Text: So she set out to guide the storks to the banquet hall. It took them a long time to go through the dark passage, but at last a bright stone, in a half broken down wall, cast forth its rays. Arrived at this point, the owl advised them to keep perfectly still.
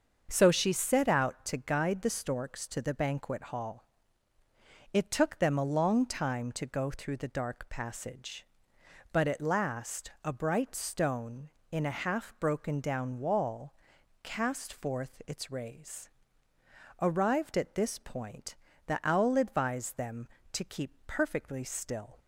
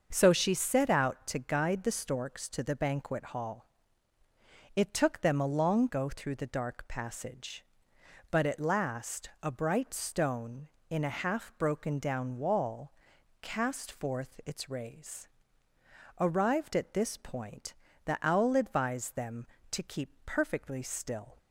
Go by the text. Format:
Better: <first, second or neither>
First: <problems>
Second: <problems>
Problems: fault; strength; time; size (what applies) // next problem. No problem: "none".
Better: first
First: starts louder than the rest; until 1.3 s; 6.5 dB // pauses between "keep" and "perfectly"; slight; at 20.9 s; 0.16 s long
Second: starts louder than the rest; until 1.1 s; 6.5 dB // skips "time to"; at 5.8 s // pauses between "keep" and "perfectly"; slight; at 20.0 s; 0.16 s long